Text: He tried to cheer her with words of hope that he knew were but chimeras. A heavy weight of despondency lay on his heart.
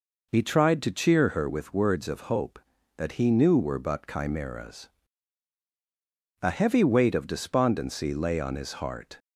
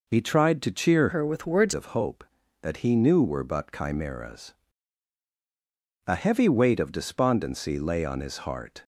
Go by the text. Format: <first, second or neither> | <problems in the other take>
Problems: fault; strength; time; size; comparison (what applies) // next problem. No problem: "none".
first | changes voice from "her" to "words"; from 1.1 to 1.7 s; 0.6 s long